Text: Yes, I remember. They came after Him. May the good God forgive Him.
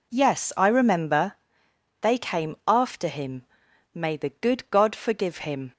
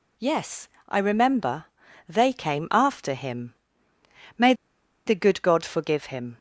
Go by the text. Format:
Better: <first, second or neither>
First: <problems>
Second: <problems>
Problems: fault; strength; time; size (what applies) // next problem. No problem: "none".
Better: first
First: none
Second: pauses between "May" and "the"; noticeable; at 4.5 s; 0.53 s long